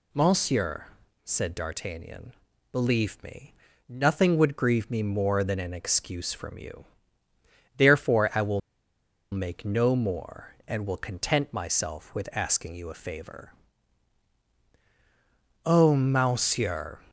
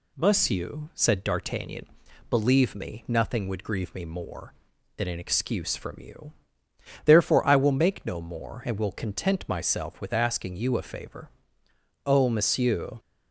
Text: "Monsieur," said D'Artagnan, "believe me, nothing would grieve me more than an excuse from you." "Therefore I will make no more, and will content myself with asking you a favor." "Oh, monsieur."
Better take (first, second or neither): second